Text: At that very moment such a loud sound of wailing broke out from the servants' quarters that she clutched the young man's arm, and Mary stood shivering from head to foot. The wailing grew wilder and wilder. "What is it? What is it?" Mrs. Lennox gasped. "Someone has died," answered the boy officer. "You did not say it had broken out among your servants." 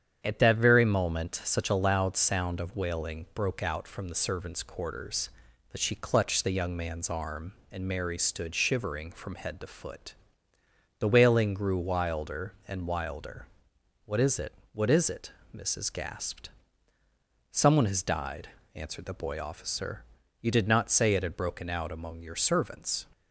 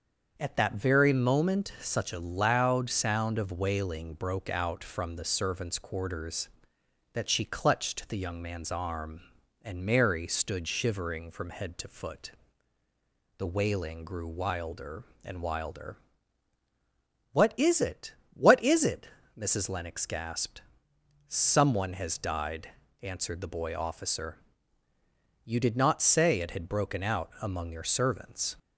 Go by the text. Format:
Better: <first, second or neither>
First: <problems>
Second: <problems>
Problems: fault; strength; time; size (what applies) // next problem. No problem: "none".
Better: second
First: starts louder than the rest; strong; until 1.2 s; 8.5 dB // skips "Lennox"; at 15.8 s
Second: starts louder than the rest; until 1.3 s; 6.5 dB